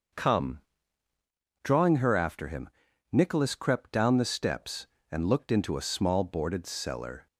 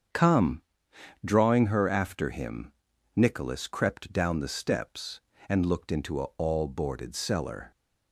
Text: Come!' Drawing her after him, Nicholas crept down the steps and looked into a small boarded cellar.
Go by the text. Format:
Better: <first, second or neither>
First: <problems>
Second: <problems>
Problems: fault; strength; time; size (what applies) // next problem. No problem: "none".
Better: first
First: starts louder than the rest; until 2.1 s; 6.5 dB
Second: starts louder than the rest; strong; until 1.7 s; 7 dB // says "all" for "small"; at 6.3 s